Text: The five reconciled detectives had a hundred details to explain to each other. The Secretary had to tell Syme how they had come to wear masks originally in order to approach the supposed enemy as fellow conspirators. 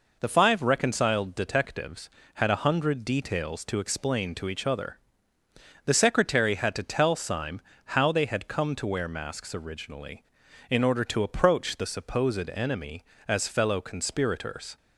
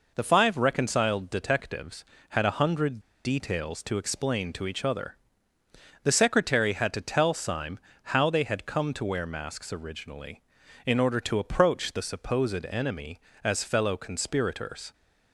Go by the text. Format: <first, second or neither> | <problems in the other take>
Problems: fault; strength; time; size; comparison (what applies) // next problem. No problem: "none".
first | pauses between "hundred" and "details"; slight; at 2.9 s; 0.25 s long // pauses between "Syme" and "how"; slight; at 7.7 s; 0.36 s long; slight in the first